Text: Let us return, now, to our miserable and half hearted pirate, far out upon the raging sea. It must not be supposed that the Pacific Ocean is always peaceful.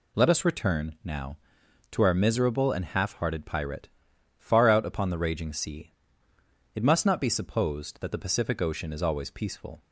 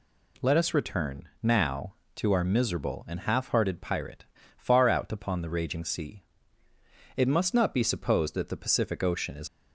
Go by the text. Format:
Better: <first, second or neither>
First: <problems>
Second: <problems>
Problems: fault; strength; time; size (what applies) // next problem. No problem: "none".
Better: first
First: none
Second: stops before "always peaceful"; at 9.4 s